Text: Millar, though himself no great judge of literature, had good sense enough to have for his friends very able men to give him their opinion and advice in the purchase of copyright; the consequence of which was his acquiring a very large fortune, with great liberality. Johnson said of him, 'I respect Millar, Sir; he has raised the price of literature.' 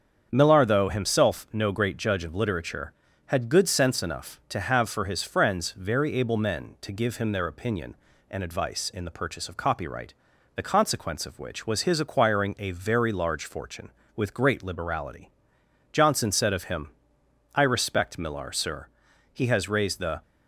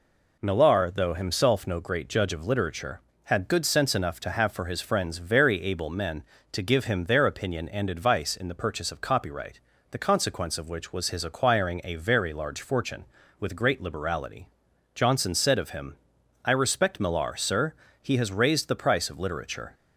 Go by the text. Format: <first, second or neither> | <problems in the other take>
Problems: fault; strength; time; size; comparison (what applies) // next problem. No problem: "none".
second | starts louder than the rest; strong; until 1.3 s; 7.5 dB // stops before "price of literature"; at 20.2 s